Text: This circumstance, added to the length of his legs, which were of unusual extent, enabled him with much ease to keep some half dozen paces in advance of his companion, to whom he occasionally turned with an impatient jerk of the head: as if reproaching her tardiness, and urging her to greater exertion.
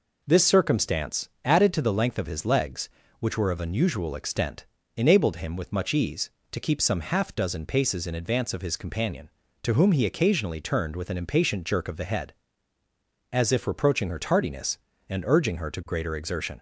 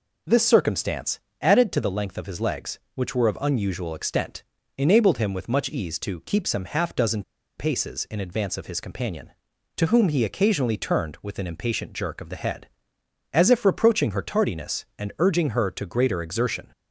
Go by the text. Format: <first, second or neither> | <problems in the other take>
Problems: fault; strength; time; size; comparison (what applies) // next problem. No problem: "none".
first | pauses between "dozen" and "paces"; slight; at 7.2 s; 0.35 s long